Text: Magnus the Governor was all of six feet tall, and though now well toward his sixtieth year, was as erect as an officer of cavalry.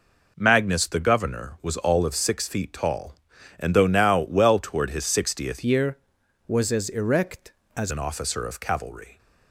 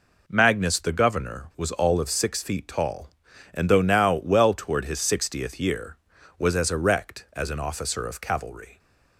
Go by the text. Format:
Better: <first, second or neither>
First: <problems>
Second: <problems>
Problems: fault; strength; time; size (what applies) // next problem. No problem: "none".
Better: second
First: changes voice from "year" to "as"; from 5.6 to 7.9 s; 2.3 s long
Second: none